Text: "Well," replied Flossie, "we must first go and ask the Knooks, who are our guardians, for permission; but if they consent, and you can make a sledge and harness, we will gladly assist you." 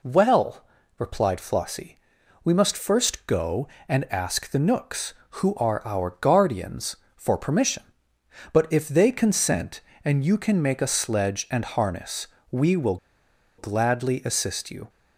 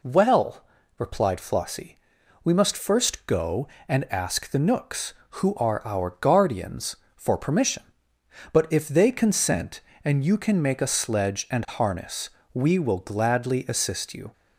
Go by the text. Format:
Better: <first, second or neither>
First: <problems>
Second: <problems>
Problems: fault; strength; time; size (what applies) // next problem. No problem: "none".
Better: second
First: pauses between "will" and "gladly"; noticeable; at 12.9 s; 0.62 s long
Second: none